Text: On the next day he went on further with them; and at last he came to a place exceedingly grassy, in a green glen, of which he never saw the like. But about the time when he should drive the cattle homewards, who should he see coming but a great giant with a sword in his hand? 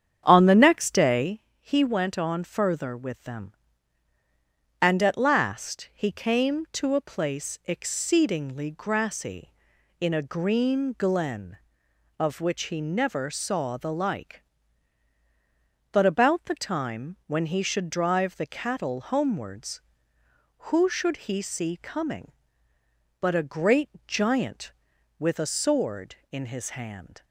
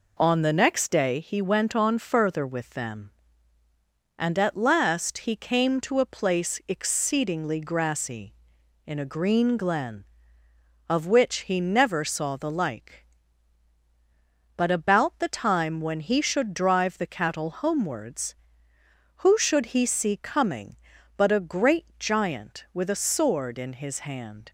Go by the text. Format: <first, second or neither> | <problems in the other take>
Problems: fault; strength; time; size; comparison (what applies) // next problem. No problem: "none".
second | starts louder than the rest; strong; until 1.5 s; 8.5 dB // pauses between "day" and "he"; slight; at 1.4 s; 0.18 s long // pauses between "great" and "giant"; slight; at 23.9 s; 0.16 s long